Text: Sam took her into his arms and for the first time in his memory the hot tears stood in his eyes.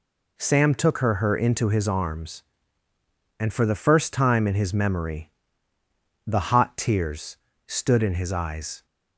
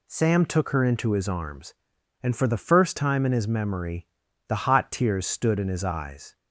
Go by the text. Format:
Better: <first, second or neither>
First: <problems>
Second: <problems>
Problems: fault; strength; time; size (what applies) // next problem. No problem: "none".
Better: second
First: says "her" twice; at 1.1 s // pauses between "memory" and "the"; noticeable; at 5.3 s; 0.96 s long // pauses between "tears" and "stood"; slight; at 7.3 s; 0.30 s long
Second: pauses between "memory" and "the"; at 4.0 s; 0.40 s long